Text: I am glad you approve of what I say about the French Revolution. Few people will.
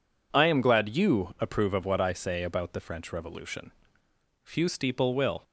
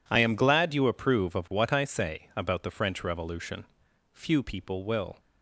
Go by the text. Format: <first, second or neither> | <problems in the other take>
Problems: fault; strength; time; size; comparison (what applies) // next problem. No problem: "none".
second | says "steeple" for "people"; at 4.6 s